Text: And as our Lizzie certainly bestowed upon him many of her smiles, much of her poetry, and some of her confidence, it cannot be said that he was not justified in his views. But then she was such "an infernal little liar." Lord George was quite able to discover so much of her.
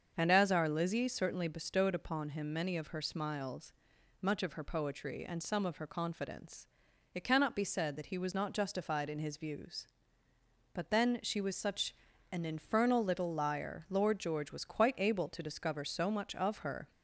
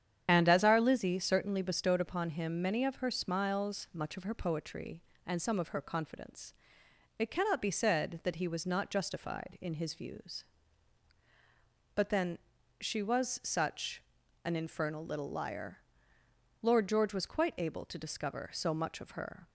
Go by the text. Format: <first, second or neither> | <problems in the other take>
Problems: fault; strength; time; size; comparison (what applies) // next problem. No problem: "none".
first | loses the start of "And"; at 0.2 s; 60 ms // starts louder than the rest; strong; until 1.2 s; 9 dB; also in the first // pauses between "then" and "she"; at 12.3 s; 0.40 s long // pauses between "such" and "an"; at 14.0 s; 0.44 s long; slight in the first